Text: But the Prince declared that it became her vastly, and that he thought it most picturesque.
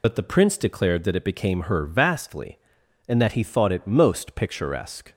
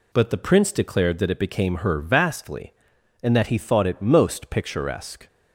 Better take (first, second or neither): second